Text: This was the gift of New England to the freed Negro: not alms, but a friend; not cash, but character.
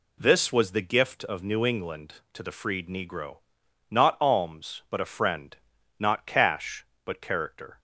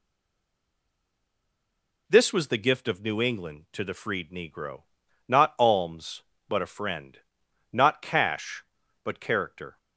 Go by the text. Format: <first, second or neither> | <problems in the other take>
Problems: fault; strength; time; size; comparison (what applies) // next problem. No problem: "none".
first | stays silent before the first word; noticeable; until 2.0 s; 2.0 s long